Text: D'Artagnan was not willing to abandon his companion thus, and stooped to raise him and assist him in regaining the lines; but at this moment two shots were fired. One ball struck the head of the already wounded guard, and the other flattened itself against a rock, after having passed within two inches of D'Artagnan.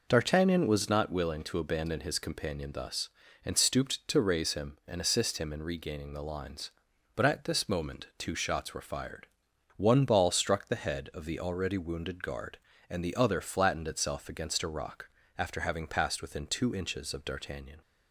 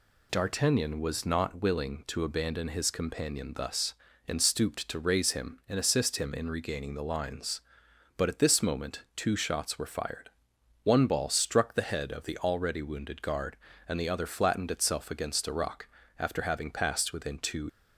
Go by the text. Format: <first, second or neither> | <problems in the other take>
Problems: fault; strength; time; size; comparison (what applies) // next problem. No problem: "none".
first | stops before "inches of D'Artagnan"; at 17.6 s